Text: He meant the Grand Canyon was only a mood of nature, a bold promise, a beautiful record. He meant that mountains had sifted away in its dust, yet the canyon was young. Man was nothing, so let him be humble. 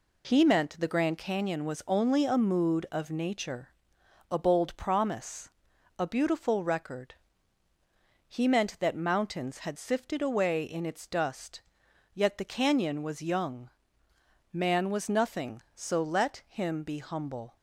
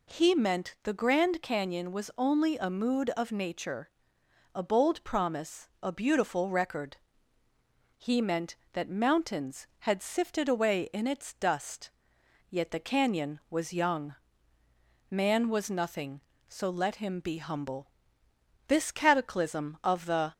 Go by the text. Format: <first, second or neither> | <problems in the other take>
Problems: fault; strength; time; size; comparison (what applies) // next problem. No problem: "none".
first | goes on to say "This cataclysm of the"; from 18.6 s on; 1.6 s long